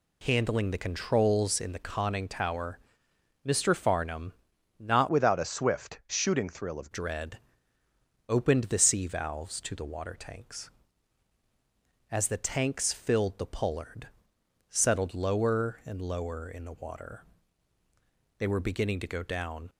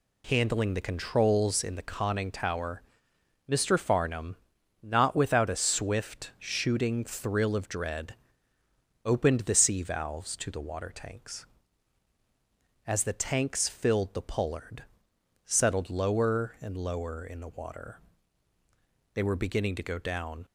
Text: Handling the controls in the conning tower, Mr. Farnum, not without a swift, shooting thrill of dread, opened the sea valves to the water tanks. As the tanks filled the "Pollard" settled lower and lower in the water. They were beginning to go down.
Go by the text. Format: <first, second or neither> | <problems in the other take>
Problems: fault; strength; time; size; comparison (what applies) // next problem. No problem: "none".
second | changes voice from "without" to "of"; from 5.0 to 6.8 s; 1.8 s long // pauses between "Pollard" and "settled"; noticeable; at 14.0 s; 0.58 s long; noticeable in the second